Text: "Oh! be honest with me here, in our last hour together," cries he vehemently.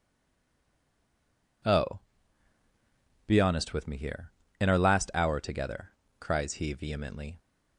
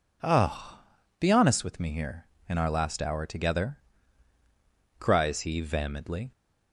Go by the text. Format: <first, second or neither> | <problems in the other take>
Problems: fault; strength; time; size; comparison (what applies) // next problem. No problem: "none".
second | stays silent before the first word; noticeable; until 1.6 s; 1.6 s long